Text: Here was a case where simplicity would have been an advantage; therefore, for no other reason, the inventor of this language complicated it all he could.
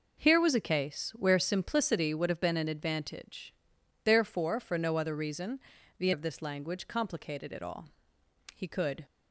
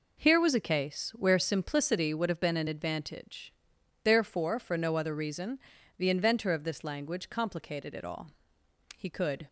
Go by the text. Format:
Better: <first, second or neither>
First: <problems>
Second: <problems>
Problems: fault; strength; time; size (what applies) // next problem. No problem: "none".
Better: second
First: skips "inventor"; at 6.1 s // pauses between "all" and "he"; noticeable; at 7.8 s; 0.64 s long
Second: pauses between "all" and "he"; noticeable; at 8.3 s; 0.64 s long